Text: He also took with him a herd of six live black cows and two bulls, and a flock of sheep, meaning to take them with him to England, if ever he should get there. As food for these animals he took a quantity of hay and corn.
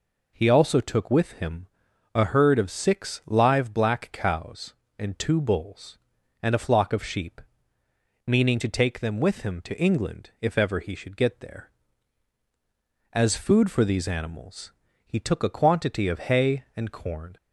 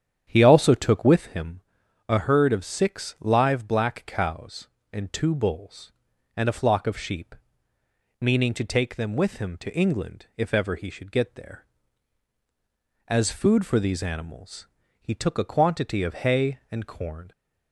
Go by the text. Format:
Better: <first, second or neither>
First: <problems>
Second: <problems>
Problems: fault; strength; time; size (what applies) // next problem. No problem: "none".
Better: first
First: pauses between "him" and "a"; at 1.6 s; 0.44 s long // pauses between "animals" and "he"; slight; at 14.7 s; 0.32 s long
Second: starts louder than the rest; strong; until 1.3 s; 9 dB // pauses between "him" and "a"; at 1.6 s; 0.44 s long // pauses between "animals" and "he"; slight; at 14.6 s; 0.32 s long